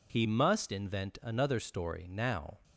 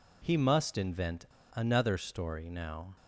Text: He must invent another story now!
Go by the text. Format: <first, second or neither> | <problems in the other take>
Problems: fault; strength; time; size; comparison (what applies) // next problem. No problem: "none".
first | pauses between "invent" and "another"; slight; at 1.2 s; 0.30 s long